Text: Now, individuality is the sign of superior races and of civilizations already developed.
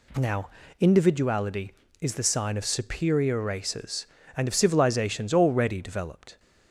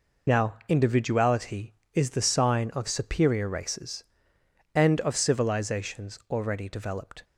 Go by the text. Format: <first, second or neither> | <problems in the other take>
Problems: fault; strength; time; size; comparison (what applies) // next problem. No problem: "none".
first | loses the start of "Now"; at 0.2 s; 65 ms